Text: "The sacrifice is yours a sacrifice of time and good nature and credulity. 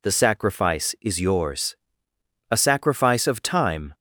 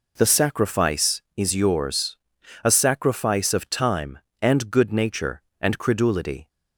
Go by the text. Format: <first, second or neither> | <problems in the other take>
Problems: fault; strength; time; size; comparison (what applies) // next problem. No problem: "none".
second | pauses between "yours" and "a"; noticeable; at 1.7 s; 0.74 s long; noticeable in the second // stops before "and good nature and credulity"; at 3.9 s